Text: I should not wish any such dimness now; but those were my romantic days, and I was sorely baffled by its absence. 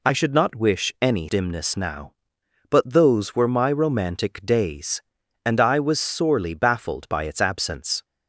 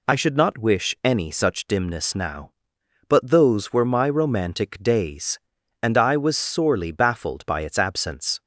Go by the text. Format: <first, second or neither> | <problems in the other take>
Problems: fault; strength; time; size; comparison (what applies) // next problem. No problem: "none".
second | skips "such"; at 1.2 s